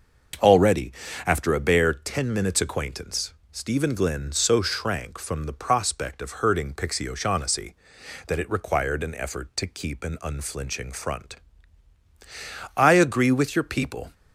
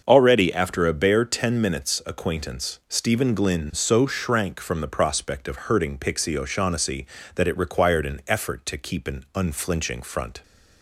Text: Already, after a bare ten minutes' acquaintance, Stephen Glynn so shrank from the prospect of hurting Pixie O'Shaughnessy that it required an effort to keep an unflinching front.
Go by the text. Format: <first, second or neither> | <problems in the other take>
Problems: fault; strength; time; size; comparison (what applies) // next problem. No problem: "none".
second | starts louder than the rest; until 1.7 s; 6.5 dB; also in the second // goes on to say "I agree with your people"; from 12.7 s on; 1.3 s long